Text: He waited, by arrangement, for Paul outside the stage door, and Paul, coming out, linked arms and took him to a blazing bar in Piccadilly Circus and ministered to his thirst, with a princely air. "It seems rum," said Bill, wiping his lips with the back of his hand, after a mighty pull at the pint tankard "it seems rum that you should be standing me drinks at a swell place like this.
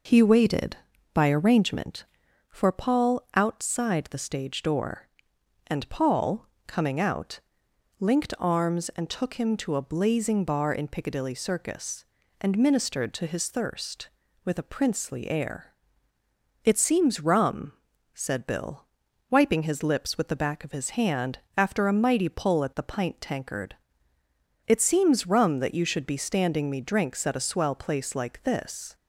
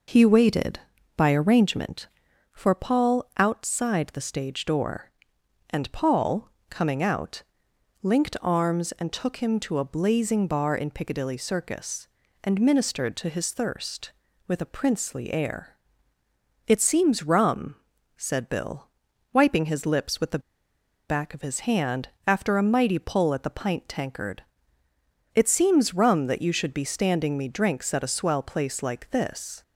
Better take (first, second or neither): first